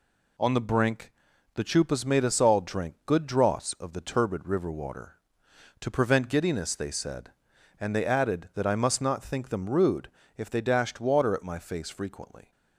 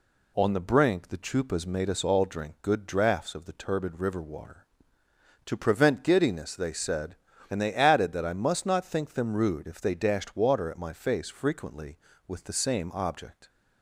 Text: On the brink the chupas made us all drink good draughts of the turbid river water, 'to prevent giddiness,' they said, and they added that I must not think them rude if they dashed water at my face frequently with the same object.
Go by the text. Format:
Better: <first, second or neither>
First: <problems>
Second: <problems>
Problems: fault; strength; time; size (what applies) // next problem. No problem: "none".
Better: second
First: pauses between "brink" and "the"; at 1.1 s; 0.44 s long // pauses between "rude" and "if"; slight; at 10.0 s; 0.26 s long // stops before "with the same object"; at 12.5 s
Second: none